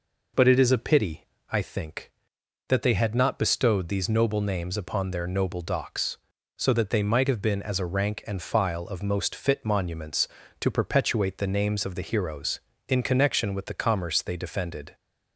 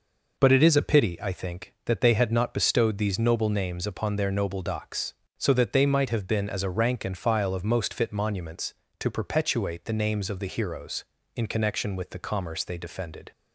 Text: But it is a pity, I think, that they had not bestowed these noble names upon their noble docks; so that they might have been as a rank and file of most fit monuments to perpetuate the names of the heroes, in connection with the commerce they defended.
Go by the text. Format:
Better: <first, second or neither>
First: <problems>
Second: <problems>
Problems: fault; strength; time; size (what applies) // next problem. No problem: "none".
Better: neither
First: none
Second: none